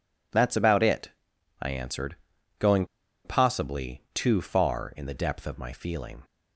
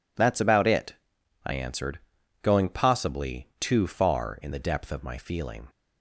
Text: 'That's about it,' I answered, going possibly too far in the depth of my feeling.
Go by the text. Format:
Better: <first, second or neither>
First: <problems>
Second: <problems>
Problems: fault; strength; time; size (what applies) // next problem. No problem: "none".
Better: second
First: pauses between "going" and "possibly"; at 2.8 s; 0.39 s long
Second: none